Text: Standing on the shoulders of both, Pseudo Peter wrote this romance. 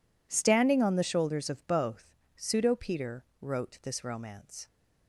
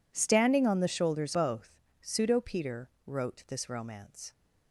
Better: first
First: pauses between "Peter" and "wrote"; slight; at 3.2 s; 0.18 s long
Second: skips "of"; at 1.3 s // pauses between "Peter" and "wrote"; slight; at 2.8 s; 0.18 s long

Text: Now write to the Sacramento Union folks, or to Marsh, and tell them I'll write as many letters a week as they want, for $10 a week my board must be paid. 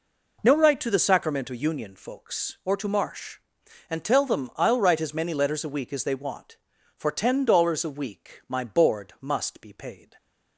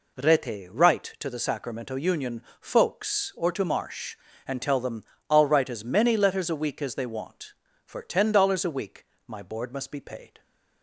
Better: first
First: none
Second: says "Rete" for "Now"; at 0.1 s // pauses between "Union" and "folks"; slight; at 2.4 s; 0.18 s long // pauses between "them" and "I'll"; slight; at 5.0 s; 0.26 s long // pauses between "week" and "my"; slight; at 9.0 s; 0.20 s long

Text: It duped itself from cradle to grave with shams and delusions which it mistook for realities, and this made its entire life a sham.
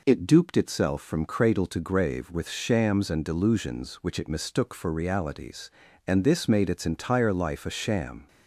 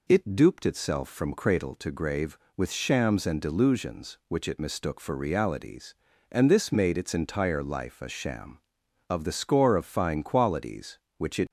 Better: first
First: none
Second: goes on to say "Of the score of fine qualities which it"; strong; from 9.0 s on; 2.4 s long

